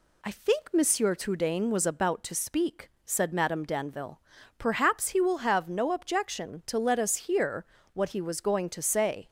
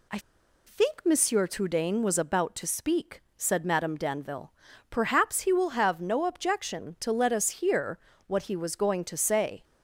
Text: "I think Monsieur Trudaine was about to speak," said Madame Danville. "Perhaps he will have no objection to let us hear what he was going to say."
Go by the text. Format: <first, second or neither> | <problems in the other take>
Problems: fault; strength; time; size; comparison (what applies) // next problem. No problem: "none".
first | pauses between "I" and "think"; noticeable; at 0.1 s; 0.47 s long // pauses between "hear" and "what"; slight; at 7.9 s; 0.26 s long; slight in the first